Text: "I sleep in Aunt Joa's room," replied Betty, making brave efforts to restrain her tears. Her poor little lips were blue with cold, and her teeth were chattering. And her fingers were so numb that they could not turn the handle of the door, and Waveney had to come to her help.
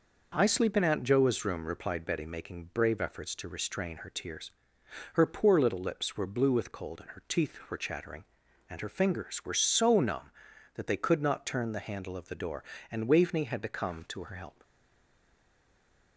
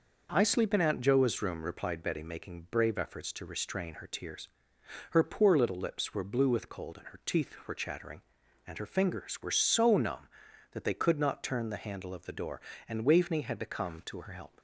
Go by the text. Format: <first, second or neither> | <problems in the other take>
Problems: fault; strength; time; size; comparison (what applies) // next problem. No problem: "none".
second | stays silent after the last word; noticeable; from 14.6 s on; 1.5 s long